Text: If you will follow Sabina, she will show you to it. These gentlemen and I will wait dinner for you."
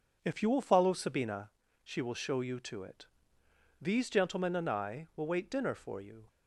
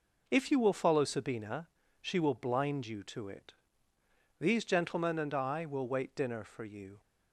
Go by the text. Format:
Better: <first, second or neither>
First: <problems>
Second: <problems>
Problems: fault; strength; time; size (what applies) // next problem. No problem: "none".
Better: first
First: none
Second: says "blind" for "show"; at 2.3 s